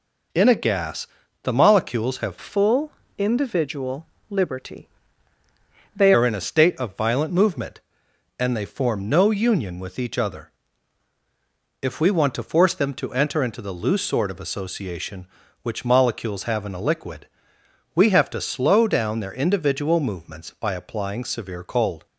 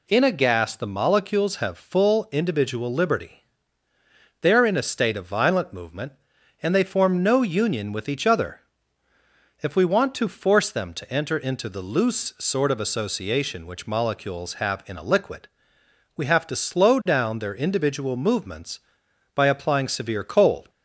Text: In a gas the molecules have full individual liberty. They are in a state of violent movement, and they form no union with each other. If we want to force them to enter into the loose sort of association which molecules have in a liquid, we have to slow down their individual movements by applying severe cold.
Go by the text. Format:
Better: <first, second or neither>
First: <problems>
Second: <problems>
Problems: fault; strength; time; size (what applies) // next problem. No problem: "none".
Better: second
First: pauses between "gas" and "the"; slight; at 1.0 s; 0.34 s long // changes voice from "full" to "They"; from 2.3 to 6.1 s; 3.8 s long // pauses between "full" and "individual"; slight; at 2.9 s; 0.26 s long // pauses between "individual" and "liberty"; slight; at 4.0 s; 0.24 s long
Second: none